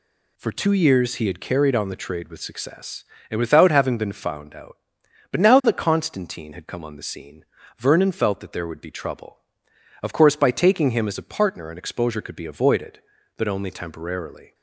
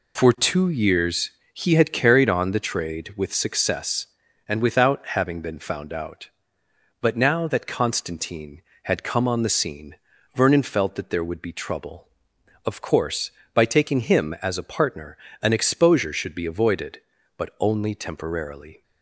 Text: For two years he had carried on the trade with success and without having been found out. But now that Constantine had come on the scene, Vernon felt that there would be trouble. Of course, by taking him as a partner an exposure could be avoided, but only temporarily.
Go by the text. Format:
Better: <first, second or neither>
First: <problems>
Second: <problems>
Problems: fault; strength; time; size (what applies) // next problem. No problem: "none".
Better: first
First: none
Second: pauses between "years" and "he"; slight; at 1.3 s; 0.22 s long // pauses between "without" and "having"; slight; at 4.9 s; 0.16 s long // pauses between "partner" and "an"; slight; at 15.1 s; 0.24 s long // says "should" for "could"; at 16.1 s